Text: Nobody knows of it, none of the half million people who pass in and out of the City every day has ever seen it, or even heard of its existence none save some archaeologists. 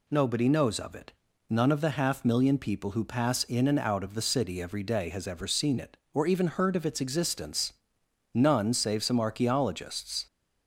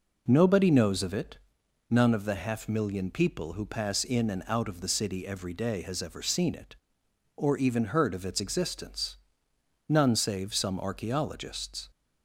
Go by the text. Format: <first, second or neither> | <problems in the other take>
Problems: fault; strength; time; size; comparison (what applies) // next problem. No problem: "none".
neither | pauses between "existence" and "none"; noticeable; the same in both